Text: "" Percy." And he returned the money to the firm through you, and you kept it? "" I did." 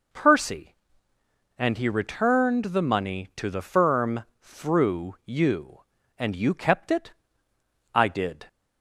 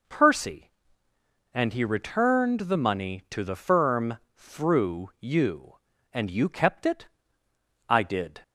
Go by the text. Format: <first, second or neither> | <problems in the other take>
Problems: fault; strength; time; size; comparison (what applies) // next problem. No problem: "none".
neither | pauses between "firm" and "through"; slight; the same in both